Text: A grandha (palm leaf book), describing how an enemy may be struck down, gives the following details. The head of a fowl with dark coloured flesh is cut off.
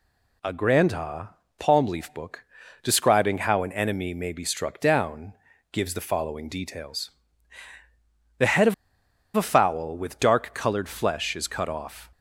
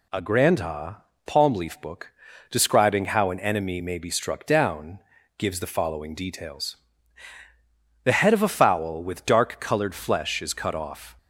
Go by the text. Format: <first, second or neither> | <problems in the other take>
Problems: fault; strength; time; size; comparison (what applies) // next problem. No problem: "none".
second | pauses between "of" and "a"; noticeable; at 8.7 s; 0.62 s long